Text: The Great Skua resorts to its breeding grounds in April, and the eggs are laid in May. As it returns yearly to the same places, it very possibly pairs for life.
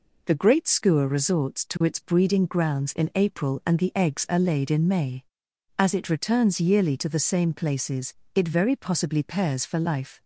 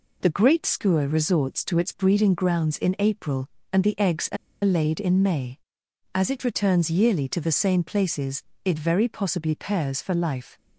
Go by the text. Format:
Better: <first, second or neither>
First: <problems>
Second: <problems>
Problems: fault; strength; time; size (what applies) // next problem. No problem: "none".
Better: first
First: none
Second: pauses between "are" and "laid"; slight; at 4.3 s; 0.28 s long